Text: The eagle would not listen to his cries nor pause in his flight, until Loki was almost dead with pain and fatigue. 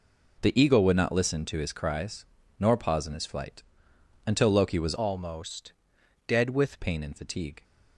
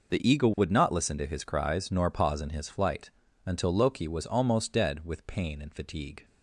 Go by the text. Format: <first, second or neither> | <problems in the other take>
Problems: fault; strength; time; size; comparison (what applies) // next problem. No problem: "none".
second | pauses between "cries" and "nor"; slight; at 2.2 s; 0.36 s long // changes voice from "almost" to "with"; from 4.9 to 6.8 s; 1.9 s long // pauses between "almost" and "dead"; noticeable; at 5.7 s; 0.52 s long